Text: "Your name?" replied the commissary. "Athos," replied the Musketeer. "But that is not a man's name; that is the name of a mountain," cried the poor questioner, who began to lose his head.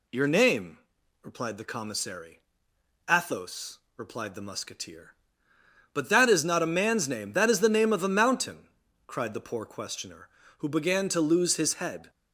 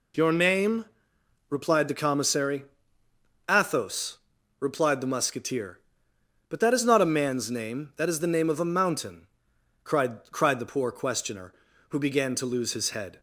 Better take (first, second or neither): first